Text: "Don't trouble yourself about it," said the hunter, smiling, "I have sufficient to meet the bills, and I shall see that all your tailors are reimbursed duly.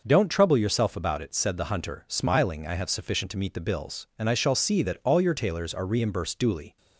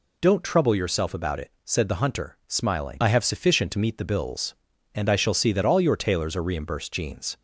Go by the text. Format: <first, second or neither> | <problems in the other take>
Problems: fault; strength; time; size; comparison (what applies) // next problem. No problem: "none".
first | says "jeans" for "duly"; at 6.9 s